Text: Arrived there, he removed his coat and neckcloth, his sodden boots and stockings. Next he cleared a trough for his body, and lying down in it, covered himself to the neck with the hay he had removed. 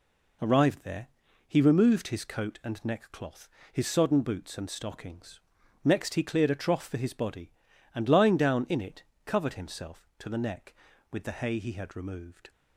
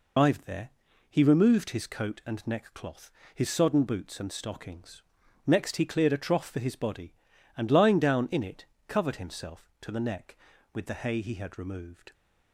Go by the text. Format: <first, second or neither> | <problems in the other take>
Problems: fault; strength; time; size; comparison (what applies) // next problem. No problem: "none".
first | loses the start of "Arrived"; at 0.1 s; 135 ms